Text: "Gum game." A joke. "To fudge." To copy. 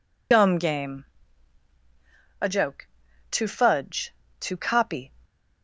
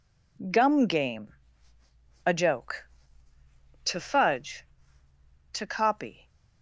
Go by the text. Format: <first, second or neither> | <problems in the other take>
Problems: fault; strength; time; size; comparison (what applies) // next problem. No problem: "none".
second | loses the start of "Gum"; at 0.3 s; 65 ms